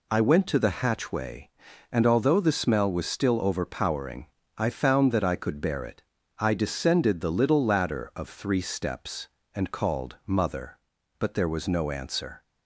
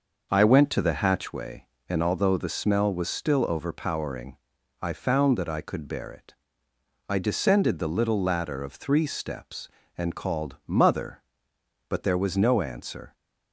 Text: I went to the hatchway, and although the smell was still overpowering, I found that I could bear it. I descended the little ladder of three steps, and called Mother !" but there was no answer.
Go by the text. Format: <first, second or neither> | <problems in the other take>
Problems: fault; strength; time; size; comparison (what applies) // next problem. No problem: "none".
first | starts louder than the rest; noticeable; until 1.4 s; 6 dB